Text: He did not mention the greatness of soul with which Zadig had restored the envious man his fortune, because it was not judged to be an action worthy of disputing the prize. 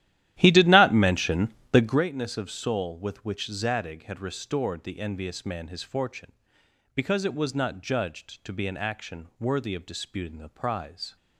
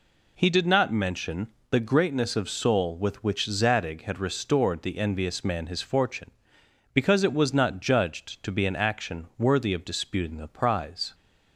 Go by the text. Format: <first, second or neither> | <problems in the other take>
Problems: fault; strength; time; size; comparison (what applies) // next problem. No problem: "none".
second | starts louder than the rest; strong; until 2.1 s; 13.5 dB // pauses between "mention" and "the"; slight; at 1.5 s; 0.20 s long; slight in the second